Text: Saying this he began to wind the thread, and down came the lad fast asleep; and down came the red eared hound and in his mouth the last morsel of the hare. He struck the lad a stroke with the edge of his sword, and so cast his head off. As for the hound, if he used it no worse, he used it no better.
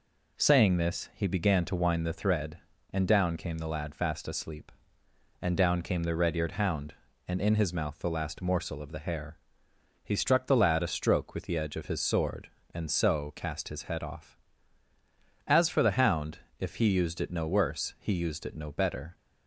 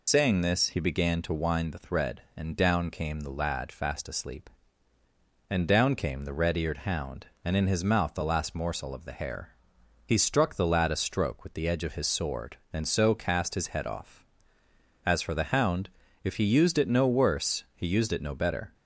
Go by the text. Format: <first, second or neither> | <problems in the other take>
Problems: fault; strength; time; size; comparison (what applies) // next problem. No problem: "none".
first | loses the start of "Saying"; at 0.0 s; 80 ms